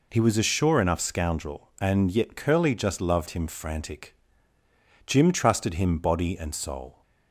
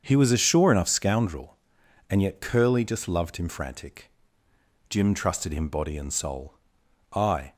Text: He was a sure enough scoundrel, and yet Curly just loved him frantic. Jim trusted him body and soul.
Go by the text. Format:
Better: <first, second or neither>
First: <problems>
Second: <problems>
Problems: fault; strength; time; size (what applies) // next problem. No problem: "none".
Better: first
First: none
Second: starts louder than the rest; until 1.0 s; 7 dB // goes on to say "I"; slight; from 7.1 s on; 0.40 s long